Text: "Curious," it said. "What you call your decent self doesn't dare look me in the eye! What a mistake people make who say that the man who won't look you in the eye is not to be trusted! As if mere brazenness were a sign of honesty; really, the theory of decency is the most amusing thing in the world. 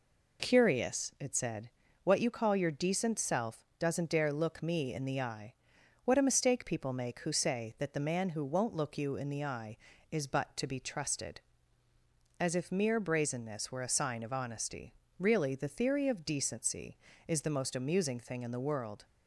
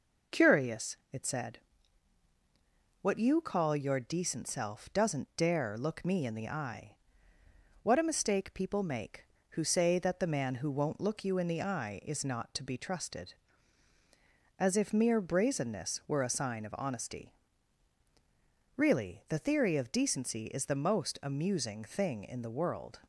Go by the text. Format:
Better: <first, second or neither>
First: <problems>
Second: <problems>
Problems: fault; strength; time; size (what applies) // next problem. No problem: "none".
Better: second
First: says "but" for "not"; at 10.2 s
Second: none